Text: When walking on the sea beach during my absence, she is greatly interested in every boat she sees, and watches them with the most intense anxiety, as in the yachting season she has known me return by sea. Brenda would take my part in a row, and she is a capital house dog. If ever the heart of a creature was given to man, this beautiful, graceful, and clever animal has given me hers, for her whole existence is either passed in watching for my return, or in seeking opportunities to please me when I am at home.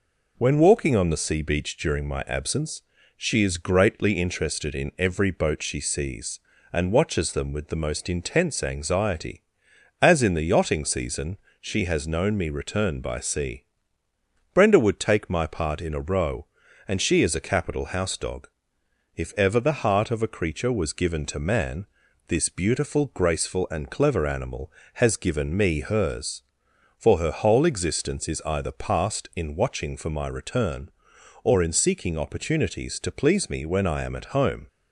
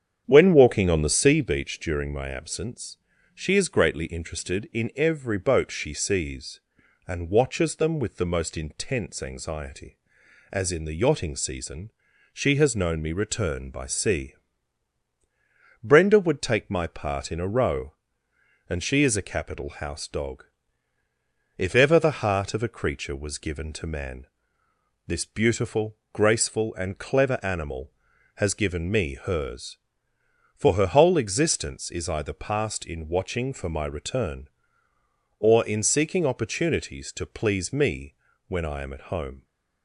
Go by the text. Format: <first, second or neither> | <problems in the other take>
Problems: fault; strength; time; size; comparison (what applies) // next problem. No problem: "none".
first | starts louder than the rest; strong; until 1.5 s; 8.5 dB // pauses between "season" and "she"; at 11.9 s; 0.42 s long; slight in the first // pauses between "me" and "when"; slight; at 38.1 s; 0.32 s long